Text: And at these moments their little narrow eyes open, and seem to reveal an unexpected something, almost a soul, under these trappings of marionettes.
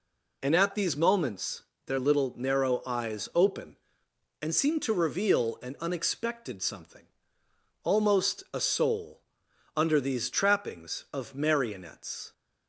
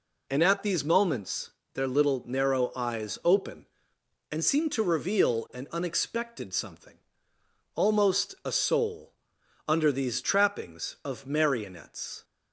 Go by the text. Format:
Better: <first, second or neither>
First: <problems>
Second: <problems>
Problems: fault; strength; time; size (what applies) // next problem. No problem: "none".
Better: neither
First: pauses between "moments" and "their"; slight; at 1.6 s; 0.24 s long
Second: pauses between "moments" and "their"; slight; at 1.4 s; 0.24 s long